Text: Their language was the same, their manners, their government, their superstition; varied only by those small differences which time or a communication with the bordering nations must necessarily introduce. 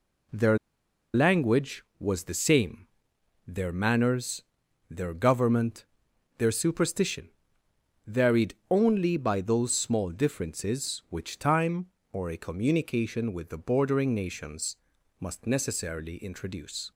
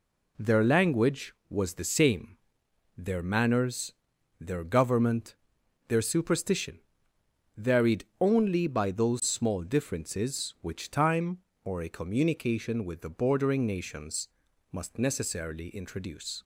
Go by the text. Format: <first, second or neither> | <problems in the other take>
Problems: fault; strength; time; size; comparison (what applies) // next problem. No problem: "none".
second | pauses between "Their" and "language"; noticeable; at 0.5 s; 0.56 s long // pauses between "varied" and "only"; slight; at 8.5 s; 0.16 s long; slight in the second // pauses between "nations" and "must"; at 14.7 s; 0.42 s long; also in the second